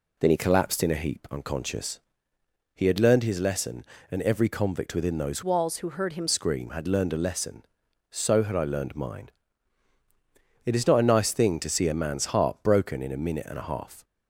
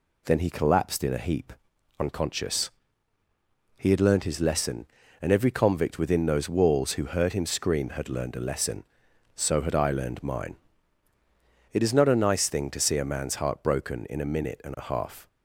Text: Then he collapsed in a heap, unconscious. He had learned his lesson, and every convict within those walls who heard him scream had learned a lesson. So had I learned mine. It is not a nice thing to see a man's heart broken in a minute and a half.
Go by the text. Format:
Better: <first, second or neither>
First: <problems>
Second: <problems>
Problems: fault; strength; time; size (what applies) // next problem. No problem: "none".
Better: second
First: changes voice from "walls" to "him"; from 5.4 to 6.2 s; 0.8 s long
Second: none